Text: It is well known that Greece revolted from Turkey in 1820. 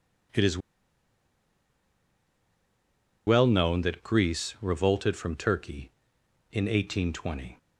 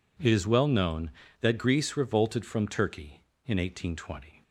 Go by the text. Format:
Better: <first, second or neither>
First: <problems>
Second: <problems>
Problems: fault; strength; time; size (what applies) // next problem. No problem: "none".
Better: second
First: pauses between "is" and "well"; strong; at 0.5 s; 2.6 s long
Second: none